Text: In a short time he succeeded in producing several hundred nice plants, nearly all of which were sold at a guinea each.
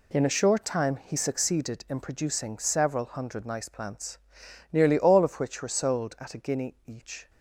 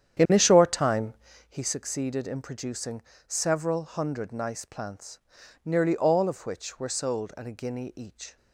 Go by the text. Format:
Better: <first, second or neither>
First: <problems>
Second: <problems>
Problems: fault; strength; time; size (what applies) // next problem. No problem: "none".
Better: first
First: none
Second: starts louder than the rest; strong; until 1.5 s; 9.5 dB // pauses between "time" and "he"; slight; at 1.1 s; 0.36 s long // pauses between "producing" and "several"; slight; at 3.0 s; 0.24 s long